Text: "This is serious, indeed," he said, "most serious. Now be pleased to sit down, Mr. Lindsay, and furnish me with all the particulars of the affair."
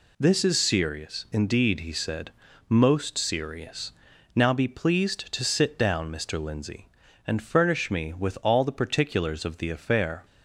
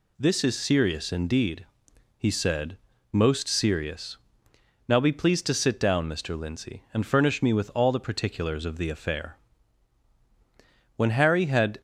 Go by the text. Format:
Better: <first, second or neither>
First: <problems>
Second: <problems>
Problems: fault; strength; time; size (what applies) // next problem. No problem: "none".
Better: first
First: none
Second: goes on to say "When Harry had"; noticeable; from 10.9 s on; 0.84 s long